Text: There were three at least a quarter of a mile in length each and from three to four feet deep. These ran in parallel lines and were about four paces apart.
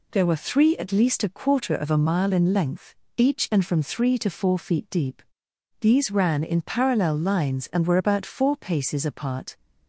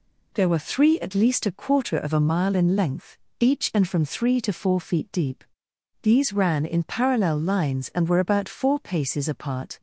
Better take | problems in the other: neither | pauses between "length" and "each"; slight; the same in both

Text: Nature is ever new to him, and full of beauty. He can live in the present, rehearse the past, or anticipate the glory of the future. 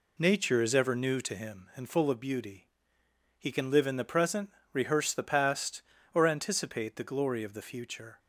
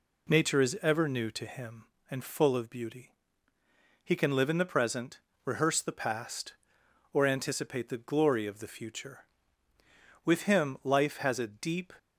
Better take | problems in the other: first | goes on to say "With him life has a deep"; strong; from 10.2 s on; 1.6 s long

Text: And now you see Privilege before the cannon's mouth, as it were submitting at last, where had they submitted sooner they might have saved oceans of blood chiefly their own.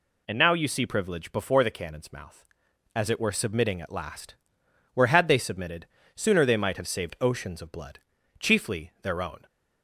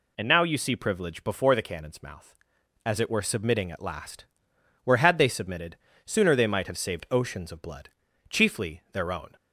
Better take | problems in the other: neither | pauses between "submitted" and "sooner"; slight; the same in both // pauses between "blood" and "chiefly"; the same in both

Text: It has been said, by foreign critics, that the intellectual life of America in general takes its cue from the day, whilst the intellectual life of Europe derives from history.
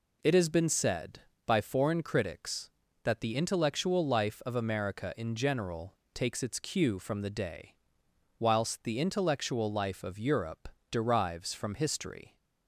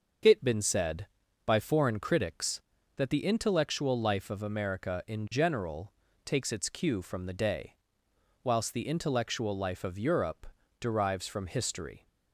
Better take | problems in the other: first | starts louder than the rest; until 1.6 s; 6.5 dB // skips "has"; at 0.4 s // pauses between "general" and "takes"; slight; at 5.9 s; 0.32 s long; slight in the first // pauses between "Europe" and "derives"; slight; at 10.4 s; 0.36 s long; slight in the first

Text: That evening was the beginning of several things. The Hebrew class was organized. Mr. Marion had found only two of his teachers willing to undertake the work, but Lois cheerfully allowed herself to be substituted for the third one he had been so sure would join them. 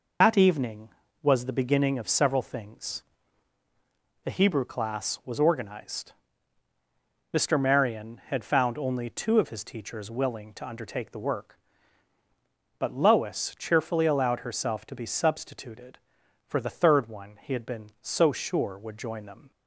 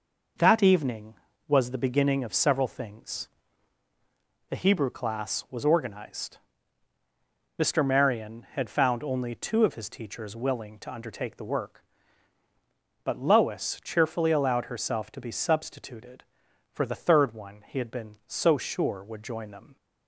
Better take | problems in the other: second | loses the start of "That"; at 0.2 s; 75 ms

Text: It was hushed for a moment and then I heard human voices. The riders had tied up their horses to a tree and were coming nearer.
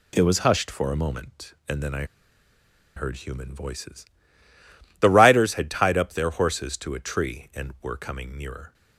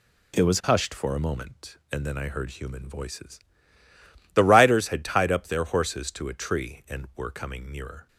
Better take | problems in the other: second | pauses between "I" and "heard"; noticeable; at 2.0 s; 0.92 s long

